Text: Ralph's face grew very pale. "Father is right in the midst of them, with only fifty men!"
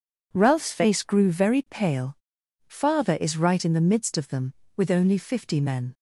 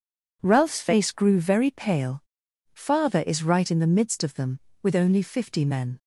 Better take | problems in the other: neither | none

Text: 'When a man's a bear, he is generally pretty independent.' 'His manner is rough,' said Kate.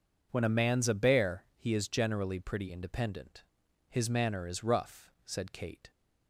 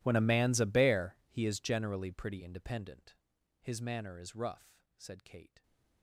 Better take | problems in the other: first | gets quieter; strong; throughout; 26.5 dB

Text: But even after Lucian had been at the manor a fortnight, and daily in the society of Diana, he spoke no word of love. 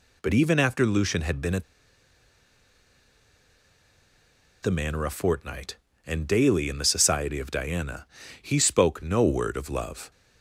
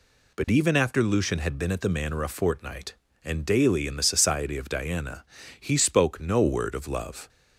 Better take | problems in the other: second | pauses between "at" and "the"; strong; at 1.6 s; 2.9 s long

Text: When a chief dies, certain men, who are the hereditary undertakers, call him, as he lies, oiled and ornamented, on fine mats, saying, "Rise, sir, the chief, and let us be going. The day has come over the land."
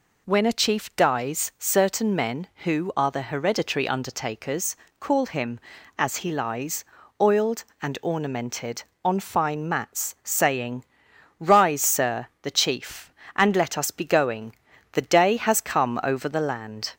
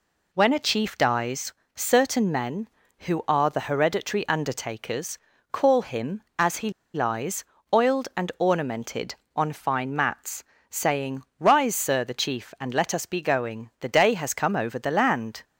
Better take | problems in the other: first | pauses between "he" and "lies"; slight; at 6.6 s; 0.24 s long

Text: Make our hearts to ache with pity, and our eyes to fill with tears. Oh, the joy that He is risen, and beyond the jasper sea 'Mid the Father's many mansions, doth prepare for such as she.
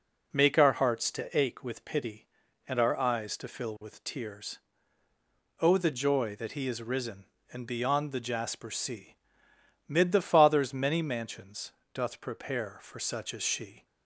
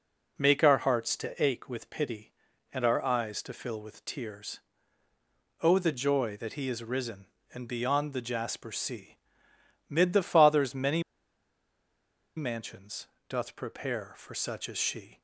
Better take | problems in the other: first | pauses between "sea" and "Mid"; noticeable; at 9.1 s; 0.72 s long; noticeable in the first // pauses between "many" and "mansions"; strong; at 11.0 s; 1.3 s long

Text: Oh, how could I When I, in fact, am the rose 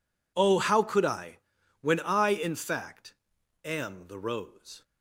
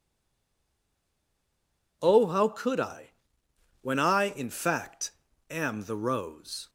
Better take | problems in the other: first | stays silent before the first word; noticeable; until 2.0 s; 2.0 s long // pauses between "I" and "When"; noticeable; at 3.0 s; 0.72 s long; also in the first

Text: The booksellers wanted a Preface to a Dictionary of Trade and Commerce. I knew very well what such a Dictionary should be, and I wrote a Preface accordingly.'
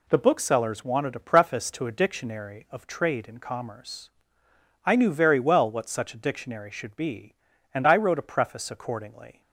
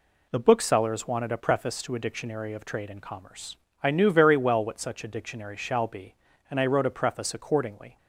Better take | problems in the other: first | says "shall" for "should"; at 5.5 s

